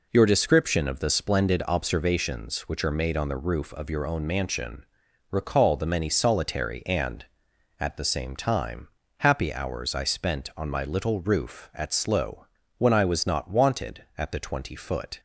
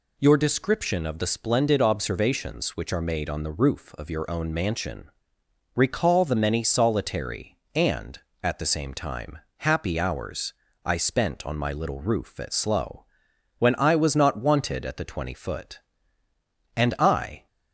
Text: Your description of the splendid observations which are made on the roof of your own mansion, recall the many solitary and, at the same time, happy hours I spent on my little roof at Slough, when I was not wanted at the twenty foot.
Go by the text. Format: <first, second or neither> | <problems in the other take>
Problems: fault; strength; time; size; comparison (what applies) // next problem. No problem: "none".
first | pauses between "hours" and "I"; slight; at 10.5 s; 0.28 s long // goes on to say "And I"; noticeable; from 16.7 s on; 0.72 s long